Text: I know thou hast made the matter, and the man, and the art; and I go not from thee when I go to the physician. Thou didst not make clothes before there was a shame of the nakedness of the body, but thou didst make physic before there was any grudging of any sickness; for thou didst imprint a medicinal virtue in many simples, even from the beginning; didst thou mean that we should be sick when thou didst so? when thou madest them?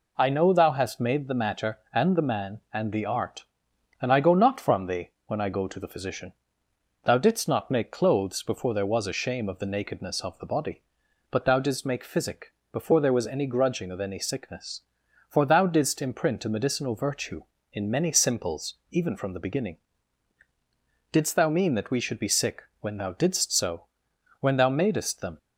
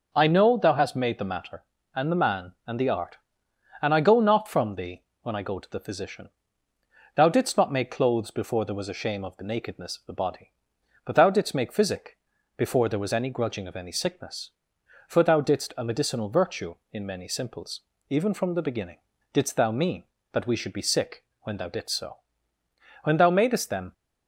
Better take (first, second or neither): first